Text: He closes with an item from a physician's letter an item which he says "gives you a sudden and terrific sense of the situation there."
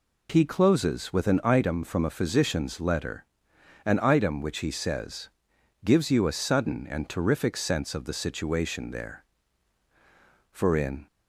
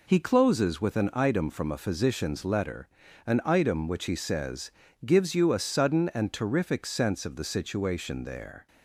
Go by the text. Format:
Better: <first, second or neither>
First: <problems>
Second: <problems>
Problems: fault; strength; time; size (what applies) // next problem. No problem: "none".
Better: second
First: pauses between "letter" and "an"; noticeable; at 3.2 s; 0.60 s long // pauses between "says" and "gives"; noticeable; at 5.2 s; 0.54 s long // goes on to say "For in"; from 10.5 s on; 0.54 s long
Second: pauses between "letter" and "an"; at 2.8 s; 0.40 s long // pauses between "says" and "gives"; slight; at 4.7 s; 0.34 s long